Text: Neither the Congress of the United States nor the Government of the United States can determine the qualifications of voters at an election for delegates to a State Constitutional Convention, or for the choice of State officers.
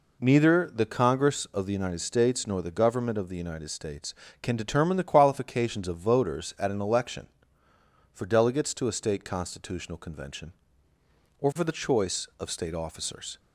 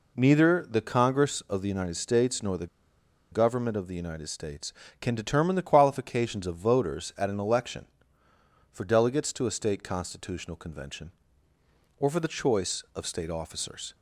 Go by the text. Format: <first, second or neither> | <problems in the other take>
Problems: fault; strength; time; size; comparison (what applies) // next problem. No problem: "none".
first | pauses between "the" and "Government"; noticeable; at 2.6 s; 0.64 s long